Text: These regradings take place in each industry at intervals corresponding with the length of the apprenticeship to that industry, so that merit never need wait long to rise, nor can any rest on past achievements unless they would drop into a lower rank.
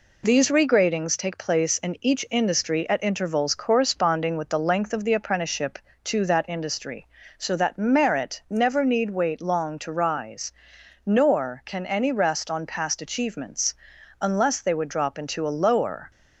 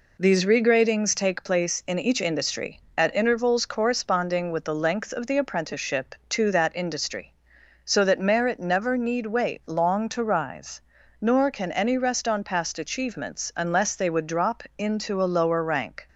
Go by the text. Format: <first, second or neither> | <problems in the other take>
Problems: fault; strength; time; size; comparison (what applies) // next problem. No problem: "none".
second | pauses between "achievements" and "unless"; at 13.7 s; 0.44 s long // stops before "rank"; at 16.1 s